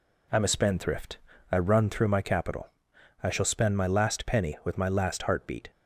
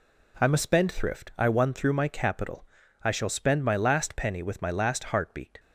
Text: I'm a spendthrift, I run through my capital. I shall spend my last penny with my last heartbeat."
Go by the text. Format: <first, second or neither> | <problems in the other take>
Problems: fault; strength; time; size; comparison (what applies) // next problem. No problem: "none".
first | says "won" for "run"; at 1.4 s